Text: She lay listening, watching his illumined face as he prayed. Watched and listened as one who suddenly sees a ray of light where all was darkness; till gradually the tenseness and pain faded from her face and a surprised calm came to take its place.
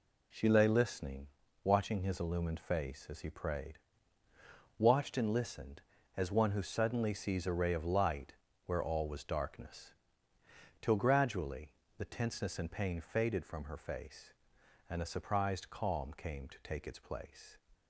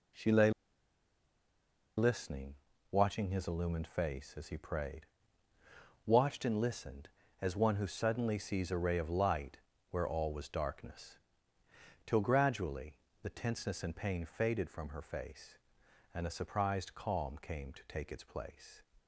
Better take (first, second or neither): first